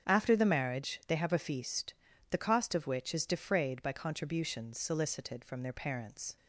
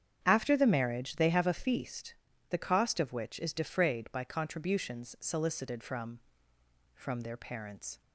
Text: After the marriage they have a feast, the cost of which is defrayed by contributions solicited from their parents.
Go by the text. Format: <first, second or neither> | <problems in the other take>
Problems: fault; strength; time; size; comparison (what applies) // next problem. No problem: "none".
first | starts louder than the rest; strong; until 1.2 s; 8.5 dB; strong in the first // says "from" twice; at 6.9 s